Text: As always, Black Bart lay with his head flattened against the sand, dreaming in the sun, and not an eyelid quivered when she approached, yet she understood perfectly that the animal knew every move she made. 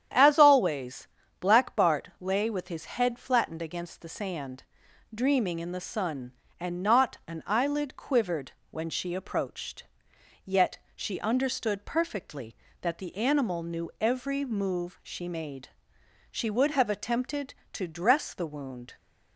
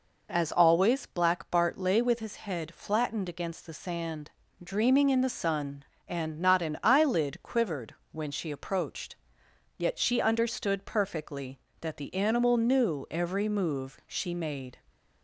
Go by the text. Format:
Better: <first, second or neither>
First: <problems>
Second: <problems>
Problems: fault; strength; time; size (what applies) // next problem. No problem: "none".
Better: second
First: starts louder than the rest; strong; until 1.4 s; 9.5 dB // pauses between "quivered" and "when"; slight; at 8.5 s; 0.18 s long // pauses between "yet" and "she"; slight; at 10.7 s; 0.18 s long // goes on to say "She would have attempted to dress the wound"; strong; from 16.3 s on; 2.6 s long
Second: pauses between "quivered" and "when"; slight; at 7.9 s; 0.16 s long